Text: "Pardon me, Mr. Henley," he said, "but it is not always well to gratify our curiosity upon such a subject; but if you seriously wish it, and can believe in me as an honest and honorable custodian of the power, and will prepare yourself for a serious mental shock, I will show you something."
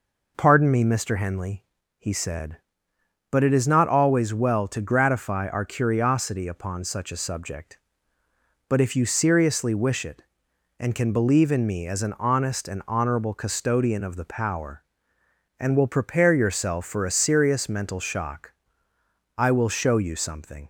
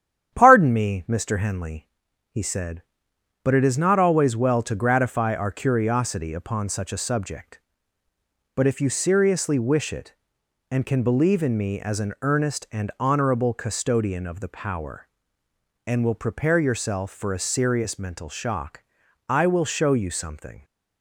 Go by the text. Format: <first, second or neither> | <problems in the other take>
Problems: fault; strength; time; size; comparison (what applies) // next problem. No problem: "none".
first | starts louder than the rest; strong; until 1.3 s; 9.5 dB // says "earnest" for "honest"; at 12.2 s